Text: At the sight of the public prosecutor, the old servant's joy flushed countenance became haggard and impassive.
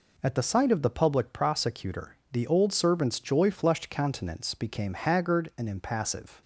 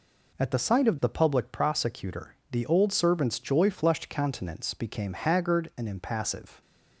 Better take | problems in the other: neither | none

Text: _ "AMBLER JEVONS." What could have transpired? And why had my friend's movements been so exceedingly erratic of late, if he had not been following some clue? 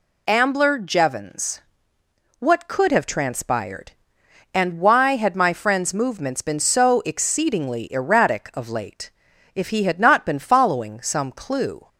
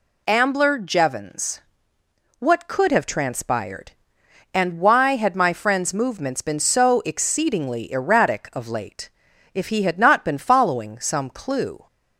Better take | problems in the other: neither | none

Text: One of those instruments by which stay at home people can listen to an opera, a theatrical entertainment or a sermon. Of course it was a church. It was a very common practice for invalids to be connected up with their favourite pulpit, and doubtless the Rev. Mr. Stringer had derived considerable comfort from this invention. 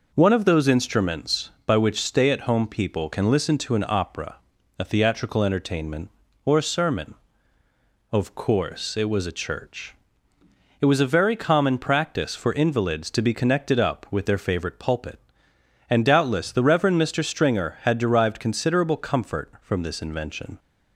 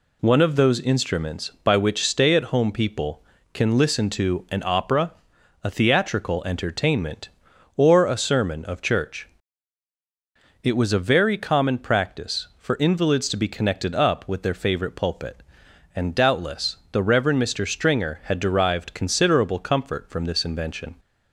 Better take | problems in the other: first | skips "course it was a"; at 8.8 s // pauses between "doubtless" and "the"; slight; at 16.7 s; 0.16 s long

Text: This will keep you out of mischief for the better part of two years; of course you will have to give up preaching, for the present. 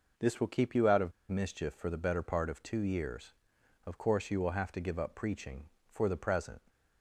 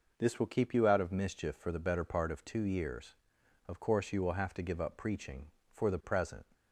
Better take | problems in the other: second | pauses between "of" and "mischief"; slight; at 1.1 s; 0.17 s long

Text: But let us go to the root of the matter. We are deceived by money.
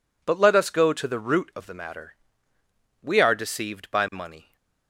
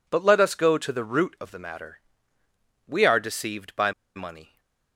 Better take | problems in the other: first | pauses between "by" and "money"; slight; at 3.9 s; 0.24 s long // stays silent after the last word; slight; from 4.4 s on; 0.5 s long

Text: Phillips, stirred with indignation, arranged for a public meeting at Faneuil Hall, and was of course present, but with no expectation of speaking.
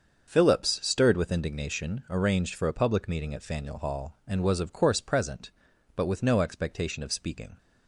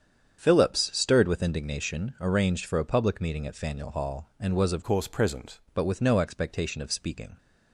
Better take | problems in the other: first | starts louder than the rest; strong; until 1.4 s; 8 dB; also in the first // changes voice from "course" to "present"; from 4.8 to 5.5 s; 0.7 s long

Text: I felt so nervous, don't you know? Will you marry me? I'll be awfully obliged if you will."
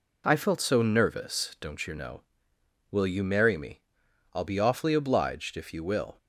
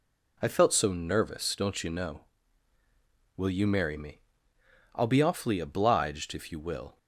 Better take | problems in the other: neither | none

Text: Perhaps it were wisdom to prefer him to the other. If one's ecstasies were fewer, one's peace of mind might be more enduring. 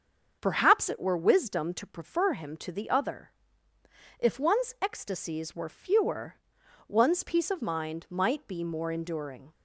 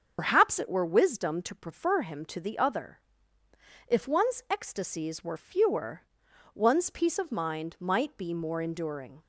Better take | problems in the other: first | loses the start of "Perhaps"; at 0.1 s; 75 ms // starts louder than the rest; until 1.2 s; 6.5 dB; also in the first

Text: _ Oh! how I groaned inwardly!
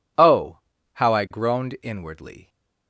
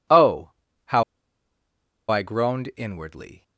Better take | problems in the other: first | pauses between "how" and "I"; at 1.0 s; 1.0 s long

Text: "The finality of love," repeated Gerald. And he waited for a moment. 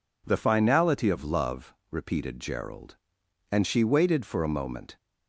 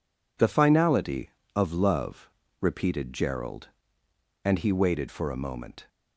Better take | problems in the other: second | says "she" for "he"; at 3.6 s

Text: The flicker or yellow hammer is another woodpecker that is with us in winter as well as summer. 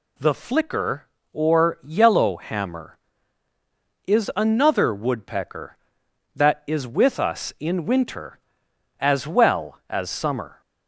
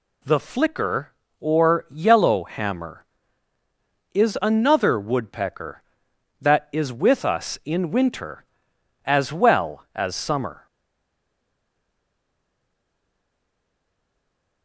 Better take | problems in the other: first | stays silent after the last word; strong; from 10.6 s on; 4.0 s long

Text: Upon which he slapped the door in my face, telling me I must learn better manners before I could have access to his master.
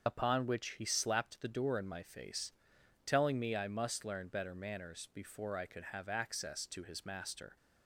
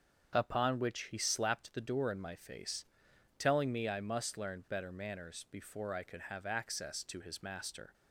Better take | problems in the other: second | loses the start of "Upon"; at 0.0 s; 60 ms // starts louder than the rest; until 1.1 s; 7 dB; strong in the second

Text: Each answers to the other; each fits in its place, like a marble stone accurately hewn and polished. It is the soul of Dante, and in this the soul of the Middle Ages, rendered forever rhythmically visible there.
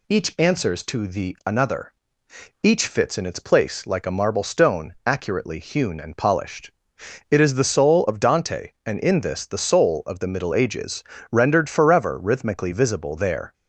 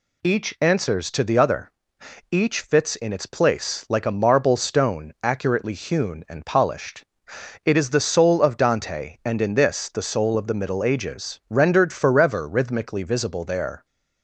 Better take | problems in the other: second | says "another" for "other"; at 1.4 s

